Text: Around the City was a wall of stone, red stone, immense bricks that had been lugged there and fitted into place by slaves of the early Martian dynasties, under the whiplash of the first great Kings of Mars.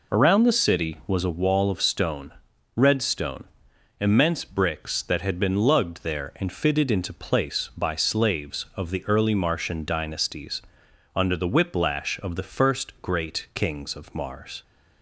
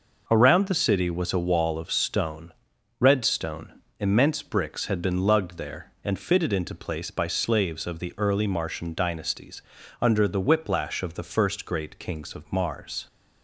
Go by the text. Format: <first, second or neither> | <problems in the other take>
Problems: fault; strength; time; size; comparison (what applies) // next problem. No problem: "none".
first | skips "that"; at 4.8 s